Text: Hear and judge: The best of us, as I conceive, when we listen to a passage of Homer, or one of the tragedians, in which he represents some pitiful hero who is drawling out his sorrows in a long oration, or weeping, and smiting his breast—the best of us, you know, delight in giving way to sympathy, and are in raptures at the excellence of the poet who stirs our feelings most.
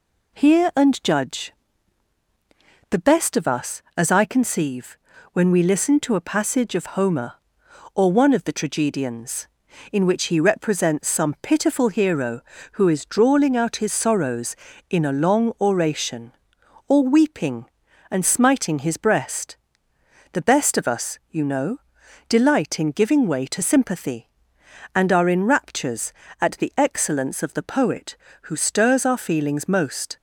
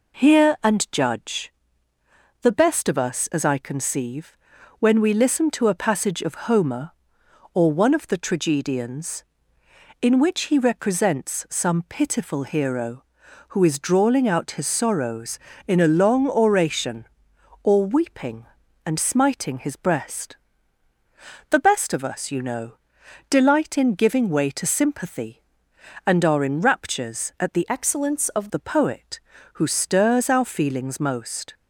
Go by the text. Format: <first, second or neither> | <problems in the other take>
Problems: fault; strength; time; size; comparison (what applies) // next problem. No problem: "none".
first | changes voice from "excellence" to "of"; from 27.6 to 28.4 s; 0.8 s long